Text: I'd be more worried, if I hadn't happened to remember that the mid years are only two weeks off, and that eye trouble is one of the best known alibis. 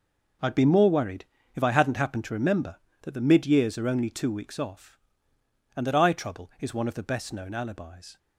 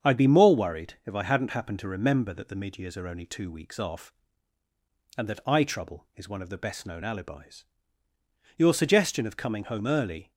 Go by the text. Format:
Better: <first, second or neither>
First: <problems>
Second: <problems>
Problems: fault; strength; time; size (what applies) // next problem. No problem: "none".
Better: first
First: none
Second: starts louder than the rest; strong; until 1.1 s; 7.5 dB // goes on to say "Your suggestion of coming home early"; strong; from 8.5 s on; 1.7 s long